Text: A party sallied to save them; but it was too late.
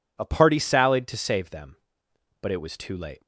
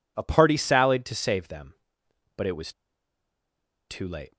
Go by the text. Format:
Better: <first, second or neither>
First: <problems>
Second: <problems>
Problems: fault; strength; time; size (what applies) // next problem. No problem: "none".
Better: first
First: none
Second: pauses between "was" and "too"; at 2.7 s; 1.1 s long